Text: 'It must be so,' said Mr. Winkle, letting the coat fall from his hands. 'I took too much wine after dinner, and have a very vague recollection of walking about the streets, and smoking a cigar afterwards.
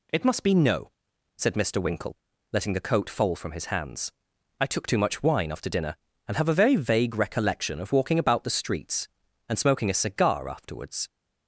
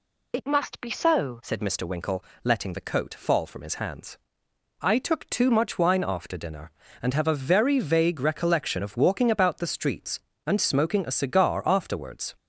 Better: second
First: says "no" for "so"; at 0.5 s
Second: none

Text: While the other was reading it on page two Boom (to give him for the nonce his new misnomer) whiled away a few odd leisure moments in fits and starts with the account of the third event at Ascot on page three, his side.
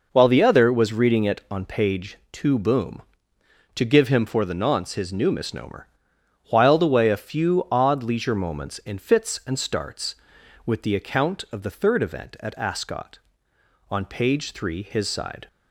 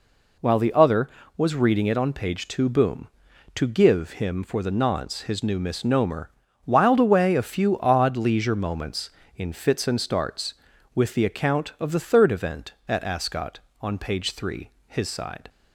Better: neither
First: none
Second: none

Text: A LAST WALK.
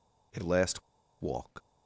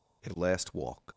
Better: second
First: pauses between "LAST" and "WALK"; at 0.8 s; 0.39 s long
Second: none

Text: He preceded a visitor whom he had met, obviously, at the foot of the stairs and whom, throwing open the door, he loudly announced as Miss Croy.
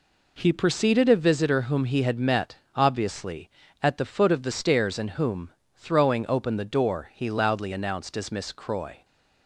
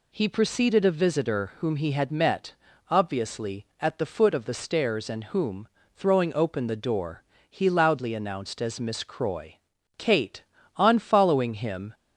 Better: first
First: none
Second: goes on to say "Kate on following him"; strong; from 9.9 s on; 1.9 s long

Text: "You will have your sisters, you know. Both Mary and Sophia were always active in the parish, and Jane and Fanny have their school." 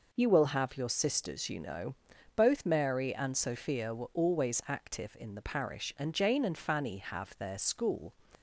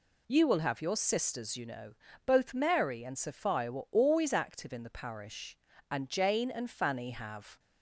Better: first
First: none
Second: stops before "their school"; at 7.5 s

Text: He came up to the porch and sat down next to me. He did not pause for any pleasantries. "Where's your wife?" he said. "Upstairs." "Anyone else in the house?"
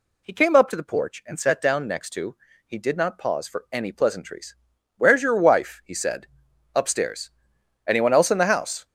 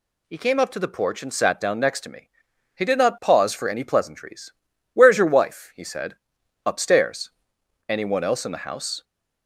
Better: second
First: skips "me"; at 2.5 s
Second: none

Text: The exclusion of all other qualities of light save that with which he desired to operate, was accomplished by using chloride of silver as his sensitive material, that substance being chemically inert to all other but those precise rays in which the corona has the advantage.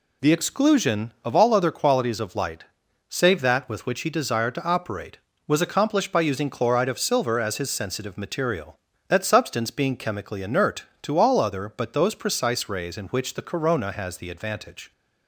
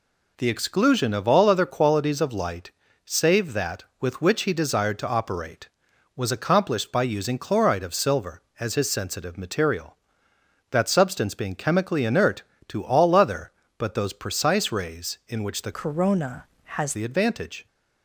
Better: first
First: pauses between "light" and "save"; at 2.6 s; 0.44 s long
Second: pauses between "light" and "save"; slight; at 2.7 s; 0.34 s long // changes voice from "corona" to "has"; from 15.7 to 16.9 s; 1.2 s long

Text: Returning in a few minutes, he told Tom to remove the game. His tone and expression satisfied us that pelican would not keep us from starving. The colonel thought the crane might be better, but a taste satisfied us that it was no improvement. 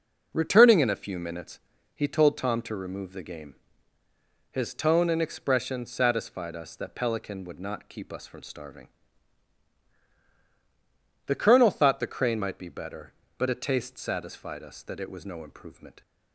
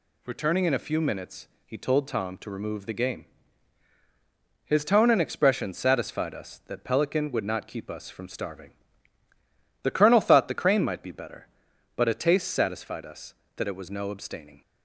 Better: first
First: none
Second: says "abstaining" for "improvement"; at 14.1 s

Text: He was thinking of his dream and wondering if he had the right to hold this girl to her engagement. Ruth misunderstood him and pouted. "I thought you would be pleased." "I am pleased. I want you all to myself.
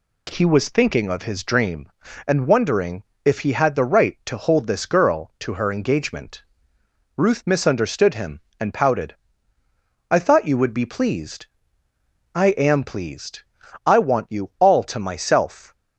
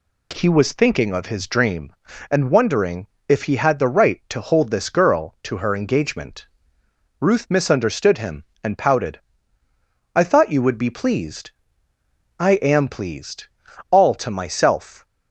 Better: first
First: pauses between "wondering" and "if"; slight; at 3.0 s; 0.22 s long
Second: pauses between "wondering" and "if"; slight; at 3.0 s; 0.22 s long // skips "I want you"; at 13.6 s

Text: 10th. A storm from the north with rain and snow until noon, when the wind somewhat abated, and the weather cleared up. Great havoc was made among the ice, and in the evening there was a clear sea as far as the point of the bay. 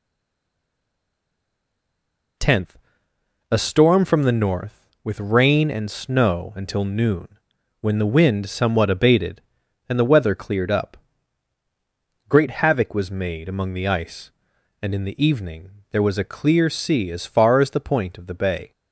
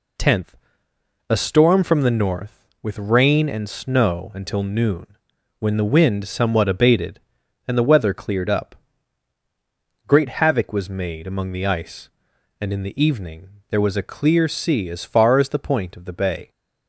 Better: second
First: stays silent before the first word; until 2.3 s; 2.3 s long // pauses between "evening" and "there"; slight; at 15.6 s; 0.22 s long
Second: pauses between "evening" and "there"; slight; at 13.4 s; 0.22 s long

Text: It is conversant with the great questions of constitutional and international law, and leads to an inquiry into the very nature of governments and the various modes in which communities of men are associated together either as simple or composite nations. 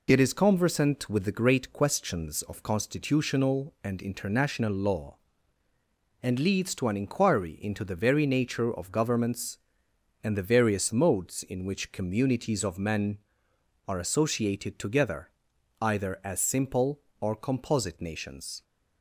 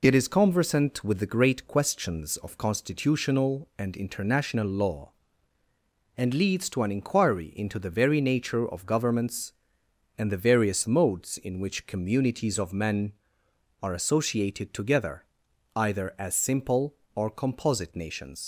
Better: first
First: pauses between "together" and "either"; noticeable; at 15.2 s; 0.50 s long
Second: pauses between "together" and "either"; noticeable; at 15.2 s; 0.50 s long // leaves "nations" unfinished; at 18.4 s; 105 ms

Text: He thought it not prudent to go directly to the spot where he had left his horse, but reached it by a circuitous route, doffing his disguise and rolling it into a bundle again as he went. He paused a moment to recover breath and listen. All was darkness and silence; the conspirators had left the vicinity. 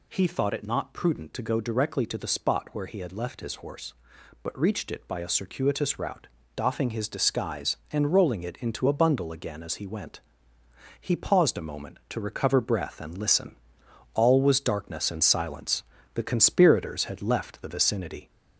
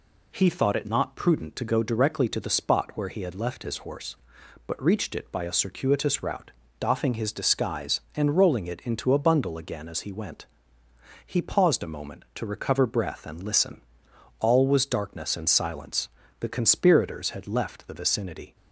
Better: second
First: gets louder; slight; throughout; 2.5 dB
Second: none

